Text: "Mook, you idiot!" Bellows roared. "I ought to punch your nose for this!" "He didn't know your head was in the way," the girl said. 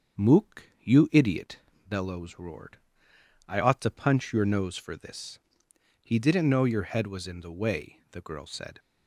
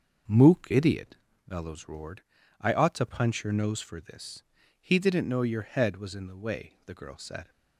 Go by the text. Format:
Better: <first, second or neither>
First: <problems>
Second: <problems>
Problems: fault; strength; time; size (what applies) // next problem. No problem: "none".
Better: first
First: starts louder than the rest; until 1.3 s; 6.5 dB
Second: starts louder than the rest; until 1.5 s; 6 dB // skips "you"; at 0.6 s